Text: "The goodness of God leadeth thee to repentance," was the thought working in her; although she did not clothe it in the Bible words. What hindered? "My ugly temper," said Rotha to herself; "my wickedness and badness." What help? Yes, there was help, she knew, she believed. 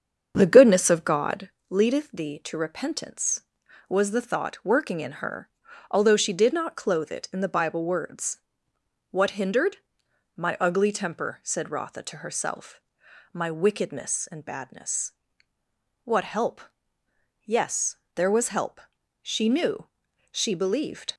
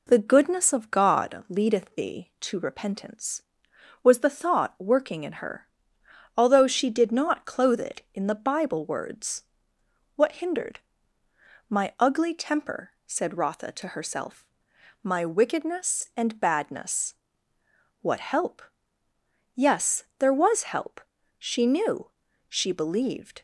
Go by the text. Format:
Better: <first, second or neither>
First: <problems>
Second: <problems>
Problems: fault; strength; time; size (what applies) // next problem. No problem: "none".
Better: second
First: starts louder than the rest; strong; until 1.5 s; 7.5 dB // pauses between "God" and "leadeth"; slight; at 1.4 s; 0.22 s long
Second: none